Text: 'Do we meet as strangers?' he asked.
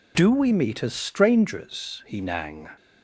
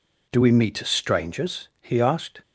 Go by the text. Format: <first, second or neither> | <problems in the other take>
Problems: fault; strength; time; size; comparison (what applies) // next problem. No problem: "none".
second | says "nang" for "asked"; at 2.2 s